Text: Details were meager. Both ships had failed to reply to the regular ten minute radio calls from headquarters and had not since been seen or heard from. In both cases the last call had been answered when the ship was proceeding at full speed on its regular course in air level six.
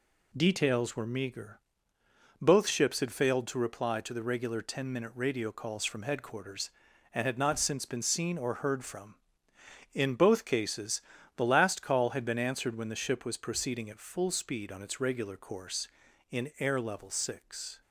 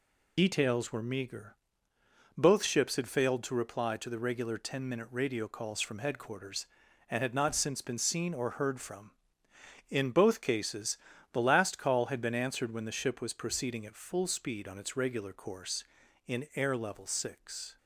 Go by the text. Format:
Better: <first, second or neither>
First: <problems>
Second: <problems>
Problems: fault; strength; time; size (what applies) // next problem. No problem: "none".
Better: first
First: pauses between "cases" and "the"; slight; at 11.0 s; 0.34 s long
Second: loses the start of "Details"; at 0.3 s; 80 ms // pauses between "cases" and "the"; slight; at 10.9 s; 0.34 s long